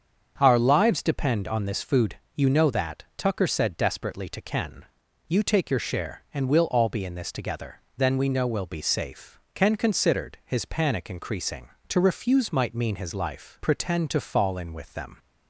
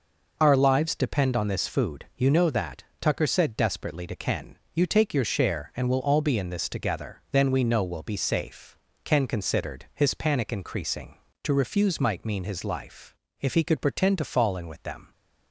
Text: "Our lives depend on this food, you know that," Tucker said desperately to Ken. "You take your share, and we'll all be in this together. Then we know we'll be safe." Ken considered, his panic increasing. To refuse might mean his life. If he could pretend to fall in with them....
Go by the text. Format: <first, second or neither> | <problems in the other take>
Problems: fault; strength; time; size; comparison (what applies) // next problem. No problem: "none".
second | starts louder than the rest; strong; until 1.3 s; 7.5 dB // skips "If he could"; at 13.6 s